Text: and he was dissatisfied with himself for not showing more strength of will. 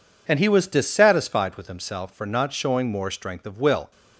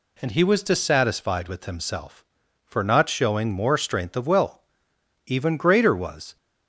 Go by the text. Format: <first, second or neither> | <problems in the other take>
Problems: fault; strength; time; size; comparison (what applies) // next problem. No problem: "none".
first | goes on to say "Even greater was"; noticeable; from 5.2 s on; 1.1 s long